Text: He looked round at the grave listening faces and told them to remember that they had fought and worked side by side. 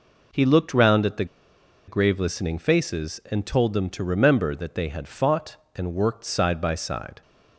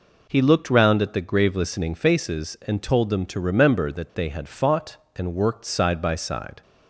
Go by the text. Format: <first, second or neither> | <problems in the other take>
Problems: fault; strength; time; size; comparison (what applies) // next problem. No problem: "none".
second | pauses between "the" and "grave"; noticeable; at 1.2 s; 0.62 s long